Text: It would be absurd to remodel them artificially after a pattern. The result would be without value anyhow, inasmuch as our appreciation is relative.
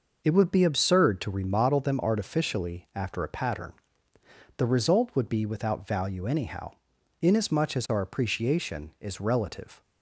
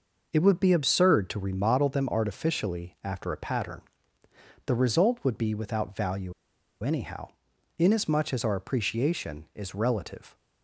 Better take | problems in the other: first | pauses between "value" and "anyhow"; noticeable; at 6.3 s; 0.50 s long

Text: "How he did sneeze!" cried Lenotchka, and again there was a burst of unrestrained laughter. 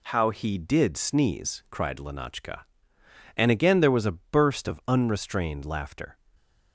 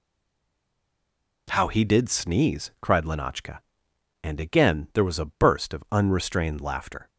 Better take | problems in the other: first | stays silent before the first word; noticeable; until 1.4 s; 1.4 s long

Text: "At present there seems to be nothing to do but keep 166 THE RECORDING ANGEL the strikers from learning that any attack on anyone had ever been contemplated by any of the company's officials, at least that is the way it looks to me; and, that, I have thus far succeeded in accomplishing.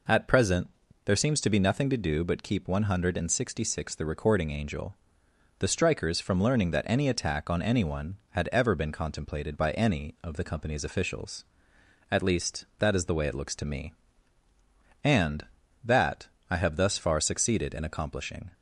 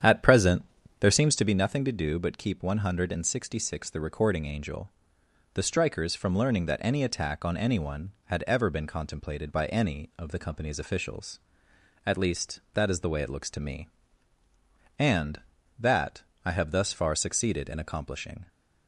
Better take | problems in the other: first | starts louder than the rest; strong; until 1.5 s; 9 dB // pauses between "present" and "there"; slight; at 0.6 s; 0.36 s long; slight in the first // pauses between "ANGEL" and "the"; noticeable; at 4.8 s; 0.64 s long; noticeable in the first

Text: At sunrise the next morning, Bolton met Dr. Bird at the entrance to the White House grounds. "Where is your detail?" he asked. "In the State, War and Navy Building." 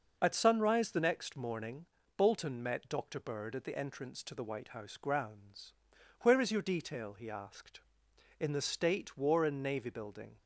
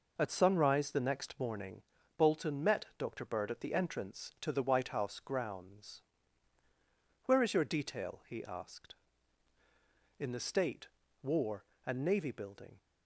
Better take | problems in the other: neither | none

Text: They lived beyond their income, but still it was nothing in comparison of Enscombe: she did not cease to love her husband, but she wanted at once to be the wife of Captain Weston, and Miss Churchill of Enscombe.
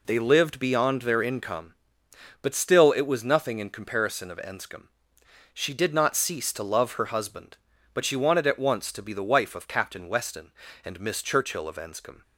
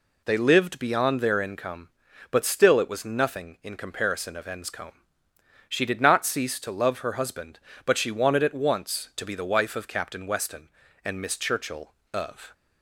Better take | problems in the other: first | stops before "Enscombe"; at 12.5 s

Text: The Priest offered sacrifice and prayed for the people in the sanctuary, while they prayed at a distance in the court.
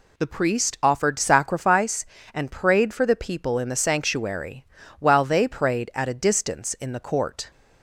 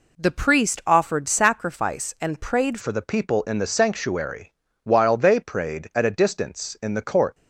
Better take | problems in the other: first | changes voice at "for"; from 2.7 s on; 4.6 s long

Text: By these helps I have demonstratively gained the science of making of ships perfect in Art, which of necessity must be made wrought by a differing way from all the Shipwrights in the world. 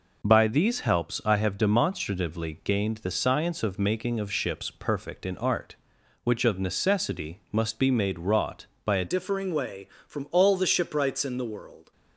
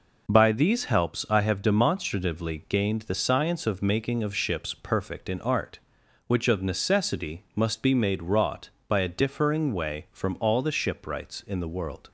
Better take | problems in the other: second | changes voice at "differing"; from 9.0 s on; 2.9 s long

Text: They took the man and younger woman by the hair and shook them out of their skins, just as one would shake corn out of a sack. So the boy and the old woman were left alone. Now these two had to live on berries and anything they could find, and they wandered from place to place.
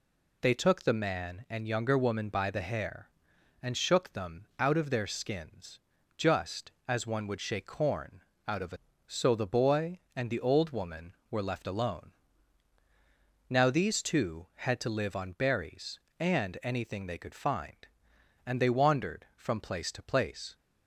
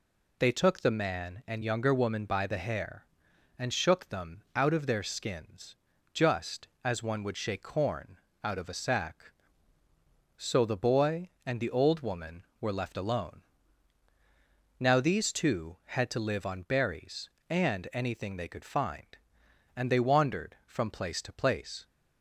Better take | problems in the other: second | pauses between "corn" and "out"; slight; at 8.2 s; 0.24 s long; slight in the second // skips "sack"; at 8.9 s

